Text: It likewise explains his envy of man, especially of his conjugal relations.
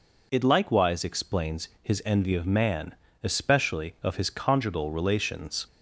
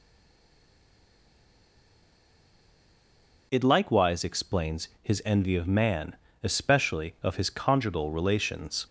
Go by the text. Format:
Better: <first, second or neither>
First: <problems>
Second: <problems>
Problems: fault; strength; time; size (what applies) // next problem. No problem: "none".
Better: first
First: pauses between "explains" and "his"; slight; at 1.6 s; 0.16 s long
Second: stays silent before the first word; strong; until 3.5 s; 3.5 s long // pauses between "explains" and "his"; slight; at 4.8 s; 0.16 s long